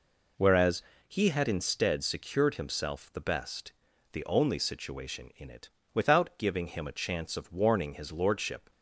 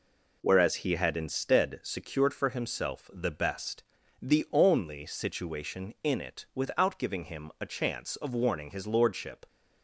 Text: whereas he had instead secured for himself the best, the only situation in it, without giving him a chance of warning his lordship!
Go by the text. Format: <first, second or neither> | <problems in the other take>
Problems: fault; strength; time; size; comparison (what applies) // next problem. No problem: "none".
second | pauses between "whereas" and "he"; slight; at 0.8 s; 0.26 s long // skips "for"; at 2.5 s